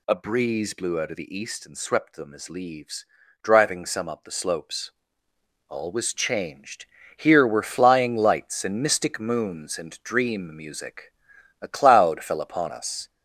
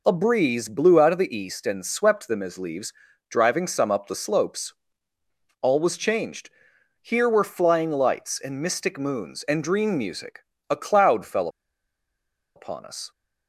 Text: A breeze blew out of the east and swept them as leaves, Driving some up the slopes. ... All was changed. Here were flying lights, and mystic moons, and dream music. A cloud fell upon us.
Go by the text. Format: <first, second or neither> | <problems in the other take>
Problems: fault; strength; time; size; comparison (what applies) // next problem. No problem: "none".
first | pauses between "fell" and "upon"; at 11.4 s; 1.0 s long